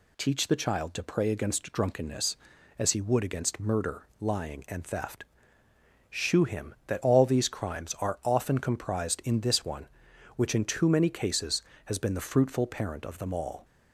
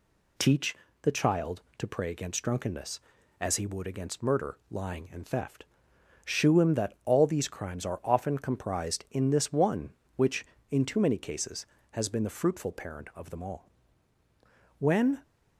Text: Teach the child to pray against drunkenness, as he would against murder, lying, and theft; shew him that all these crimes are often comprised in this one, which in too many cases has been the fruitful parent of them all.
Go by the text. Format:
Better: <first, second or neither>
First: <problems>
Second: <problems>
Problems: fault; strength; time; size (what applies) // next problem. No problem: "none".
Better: first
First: none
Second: pauses between "Teach" and "the"; slight; at 0.7 s; 0.26 s long // goes on to say "When"; slight; from 14.7 s on; 0.44 s long